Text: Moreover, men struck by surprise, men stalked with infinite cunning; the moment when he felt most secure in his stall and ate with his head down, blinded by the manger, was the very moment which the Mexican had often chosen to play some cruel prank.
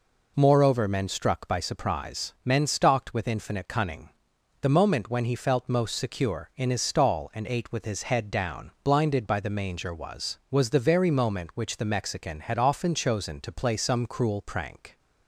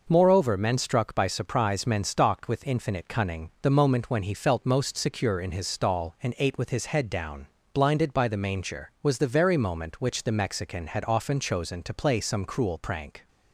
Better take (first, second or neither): second